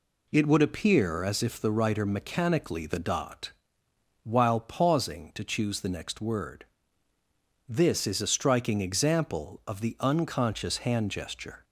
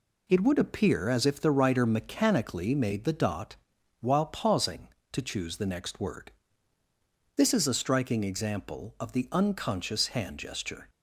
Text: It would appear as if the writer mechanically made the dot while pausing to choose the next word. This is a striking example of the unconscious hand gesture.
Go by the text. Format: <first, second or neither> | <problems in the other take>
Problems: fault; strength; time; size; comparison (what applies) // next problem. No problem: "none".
second | skips "made"; at 2.8 s // pauses between "dot" and "while"; noticeable; at 3.5 s; 0.72 s long; noticeable in the second